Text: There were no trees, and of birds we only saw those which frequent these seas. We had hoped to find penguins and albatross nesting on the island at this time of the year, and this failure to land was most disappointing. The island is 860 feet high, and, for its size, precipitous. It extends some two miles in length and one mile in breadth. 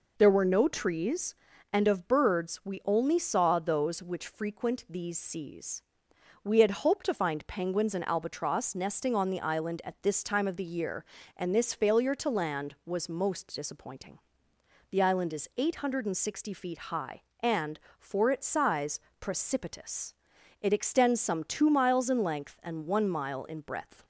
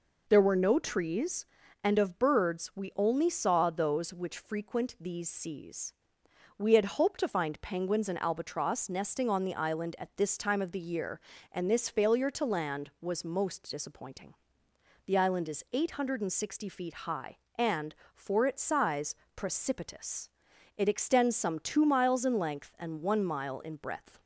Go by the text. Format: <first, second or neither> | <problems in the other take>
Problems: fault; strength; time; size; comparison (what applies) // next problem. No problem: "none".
neither | none